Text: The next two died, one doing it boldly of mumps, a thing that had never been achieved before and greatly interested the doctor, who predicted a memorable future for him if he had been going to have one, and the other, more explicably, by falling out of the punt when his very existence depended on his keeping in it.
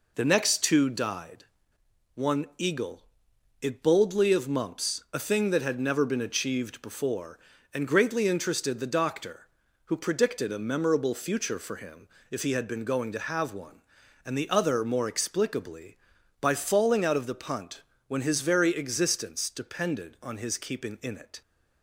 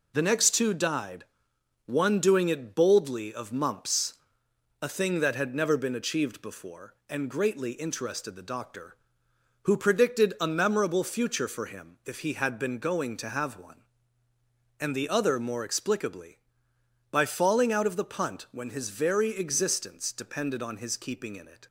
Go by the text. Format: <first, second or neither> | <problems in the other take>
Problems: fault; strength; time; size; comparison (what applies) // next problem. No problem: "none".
second | says "eagle" for "doing"; at 2.5 s // pauses between "him" and "if"; slight; at 12.0 s; 0.22 s long // pauses between "punt" and "when"; slight; at 17.8 s; 0.26 s long